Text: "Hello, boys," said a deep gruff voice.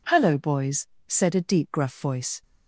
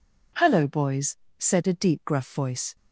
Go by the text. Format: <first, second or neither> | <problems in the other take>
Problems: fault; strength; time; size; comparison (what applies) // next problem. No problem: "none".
neither | none